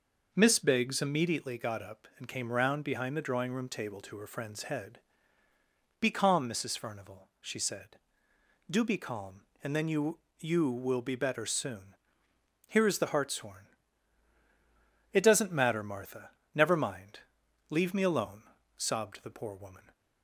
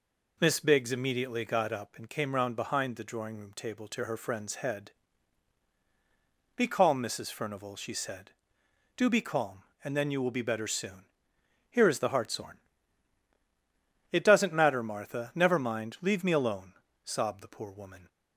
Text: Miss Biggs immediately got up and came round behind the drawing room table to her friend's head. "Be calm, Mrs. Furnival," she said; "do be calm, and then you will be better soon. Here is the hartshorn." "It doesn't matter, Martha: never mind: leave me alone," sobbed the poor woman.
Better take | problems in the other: second | says "you" twice; at 10.3 s

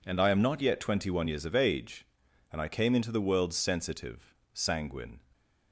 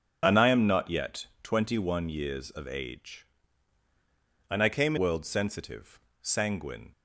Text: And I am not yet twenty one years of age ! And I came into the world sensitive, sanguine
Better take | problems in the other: first | starts louder than the rest; strong; until 1.2 s; 7 dB // pauses between "yet" and "twenty"; slight; at 1.2 s; 0.16 s long // skips "into the"; at 4.9 s

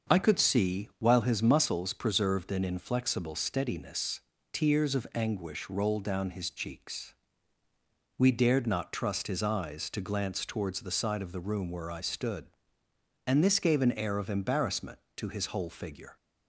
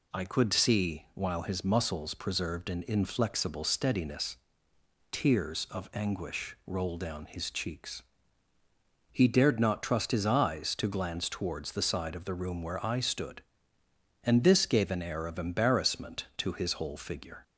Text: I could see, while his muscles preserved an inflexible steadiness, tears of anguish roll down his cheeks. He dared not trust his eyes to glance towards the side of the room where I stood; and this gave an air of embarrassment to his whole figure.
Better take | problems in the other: second | starts louder than the rest; until 1.2 s; 6.5 dB // says "We" for "He"; at 8.1 s

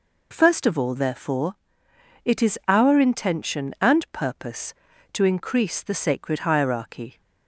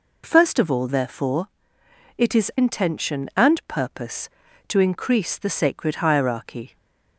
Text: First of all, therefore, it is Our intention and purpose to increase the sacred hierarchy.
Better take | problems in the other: first | skips "Our"; at 2.5 s // stays silent after the last word; slight; from 6.6 s on; 0.5 s long

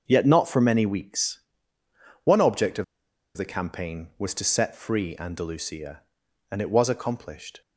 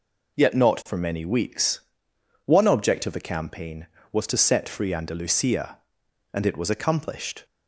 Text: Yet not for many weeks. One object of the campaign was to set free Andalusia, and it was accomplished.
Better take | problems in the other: second | starts louder than the rest; until 1.0 s; 6 dB // pauses between "of" and "the"; noticeable; at 2.8 s; 0.52 s long

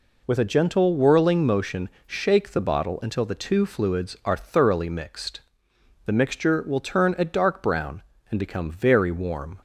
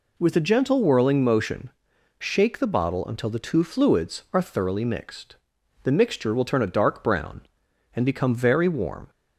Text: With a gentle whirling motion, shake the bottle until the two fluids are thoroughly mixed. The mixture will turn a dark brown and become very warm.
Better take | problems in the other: neither | none

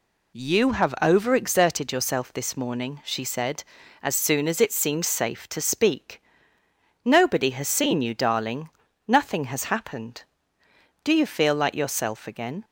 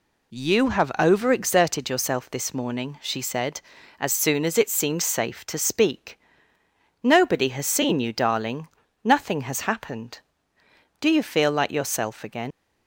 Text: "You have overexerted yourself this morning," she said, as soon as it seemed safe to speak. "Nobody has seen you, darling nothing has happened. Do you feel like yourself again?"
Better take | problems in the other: first | pauses between "darling" and "nothing"; slight; at 8.6 s; 0.34 s long; slight in the first // leaves "again" unfinished; at 12.5 s; 100 ms

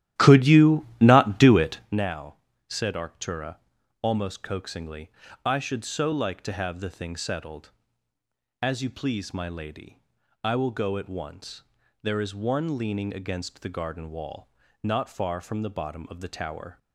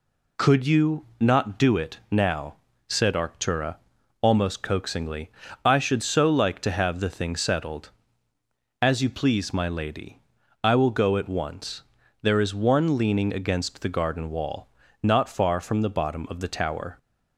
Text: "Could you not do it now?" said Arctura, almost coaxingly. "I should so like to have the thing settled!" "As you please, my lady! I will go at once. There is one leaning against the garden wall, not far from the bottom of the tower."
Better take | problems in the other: second | starts louder than the rest; strong; until 2.0 s; 13 dB

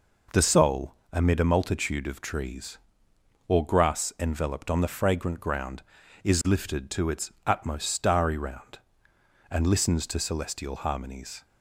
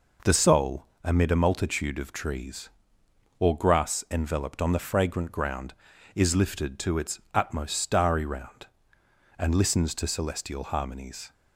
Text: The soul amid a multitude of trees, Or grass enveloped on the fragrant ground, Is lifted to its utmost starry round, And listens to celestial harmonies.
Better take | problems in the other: neither | pauses between "soul" and "amid"; slight; the same in both

